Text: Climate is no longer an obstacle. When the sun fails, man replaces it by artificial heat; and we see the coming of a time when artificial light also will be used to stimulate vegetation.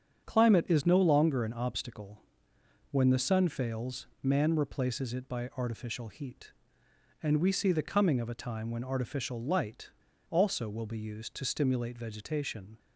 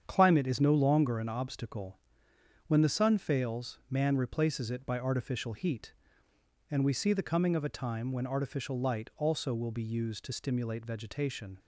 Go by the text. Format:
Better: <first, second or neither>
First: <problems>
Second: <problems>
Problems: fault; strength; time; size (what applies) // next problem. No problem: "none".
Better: second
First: starts louder than the rest; strong; until 1.2 s; 8 dB // pauses between "light" and "also"; at 9.8 s; 0.40 s long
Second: starts louder than the rest; strong; until 1.0 s; 8 dB